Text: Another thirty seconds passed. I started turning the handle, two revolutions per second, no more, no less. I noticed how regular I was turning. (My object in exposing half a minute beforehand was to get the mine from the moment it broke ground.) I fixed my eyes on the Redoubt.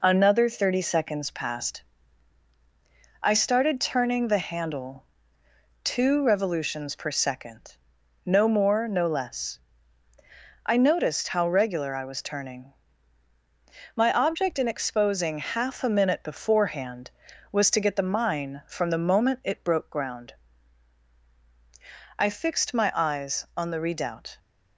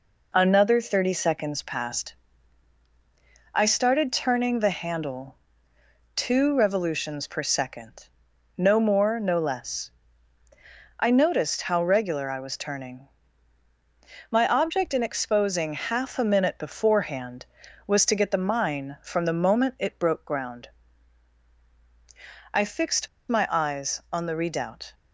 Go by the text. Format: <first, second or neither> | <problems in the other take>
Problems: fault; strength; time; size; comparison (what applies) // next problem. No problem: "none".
first | pauses between "fixed" and "my"; slight; at 23.0 s; 0.21 s long